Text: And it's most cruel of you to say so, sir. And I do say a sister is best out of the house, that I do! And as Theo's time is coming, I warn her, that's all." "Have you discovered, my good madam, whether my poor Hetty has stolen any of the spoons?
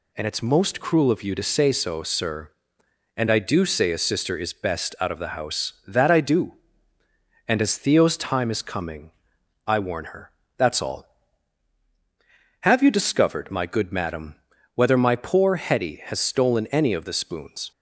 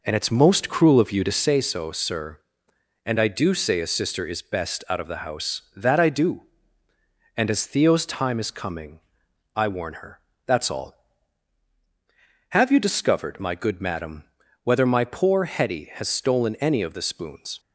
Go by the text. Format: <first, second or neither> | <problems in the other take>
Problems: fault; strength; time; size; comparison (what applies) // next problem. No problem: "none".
first | starts louder than the rest; noticeable; until 1.5 s; 4.5 dB